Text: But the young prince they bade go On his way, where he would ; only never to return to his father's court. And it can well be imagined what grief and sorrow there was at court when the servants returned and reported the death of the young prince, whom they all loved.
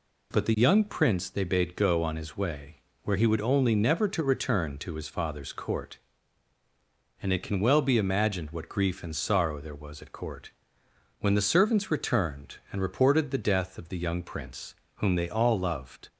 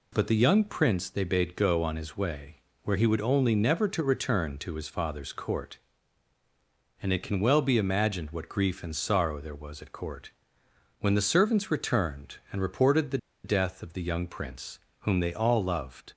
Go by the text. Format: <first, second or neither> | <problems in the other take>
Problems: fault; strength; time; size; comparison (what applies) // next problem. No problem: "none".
first | pauses between "court" and "when"; noticeable; at 10.2 s; 0.70 s long; noticeable in the first // pauses between "the" and "death"; slight; at 13.1 s; 0.26 s long